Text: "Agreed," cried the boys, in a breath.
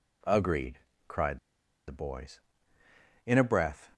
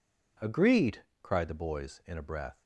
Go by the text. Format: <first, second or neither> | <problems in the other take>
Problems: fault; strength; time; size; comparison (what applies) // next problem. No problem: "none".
second | pauses between "cried" and "the"; noticeable; at 1.3 s; 0.48 s long